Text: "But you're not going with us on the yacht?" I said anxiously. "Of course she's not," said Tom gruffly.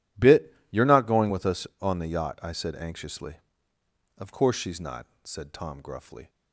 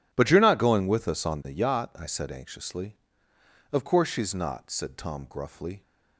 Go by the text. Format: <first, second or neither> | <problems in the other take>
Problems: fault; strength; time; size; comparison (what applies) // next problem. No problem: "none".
second | says "Bit" for "But"; at 0.1 s